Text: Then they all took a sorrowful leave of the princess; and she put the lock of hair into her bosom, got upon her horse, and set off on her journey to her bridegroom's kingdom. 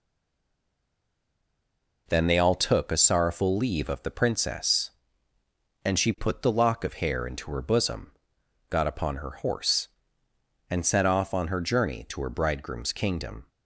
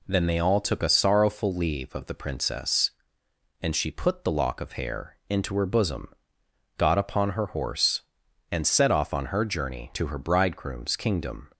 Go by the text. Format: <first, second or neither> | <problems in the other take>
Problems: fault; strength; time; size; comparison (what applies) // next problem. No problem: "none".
second | stays silent before the first word; noticeable; until 2.0 s; 2.0 s long